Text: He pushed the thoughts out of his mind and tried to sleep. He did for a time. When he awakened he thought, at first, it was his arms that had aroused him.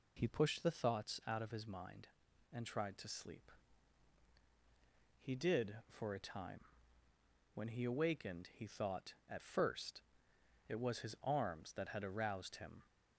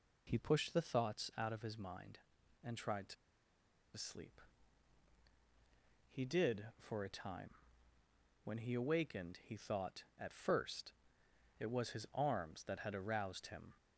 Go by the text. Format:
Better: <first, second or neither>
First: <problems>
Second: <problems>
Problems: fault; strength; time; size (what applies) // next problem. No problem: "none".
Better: first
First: none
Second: pauses between "to" and "sleep"; noticeable; at 3.1 s; 0.81 s long